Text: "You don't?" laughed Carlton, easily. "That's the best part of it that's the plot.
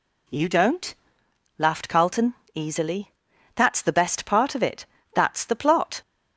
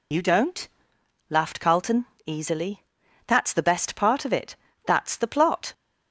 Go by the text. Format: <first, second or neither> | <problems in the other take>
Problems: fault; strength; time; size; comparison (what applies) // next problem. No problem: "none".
first | loses the start of "You"; at 0.1 s; 90 ms // pauses between "it" and "that's"; slight; at 4.5 s; 0.30 s long; slight in the first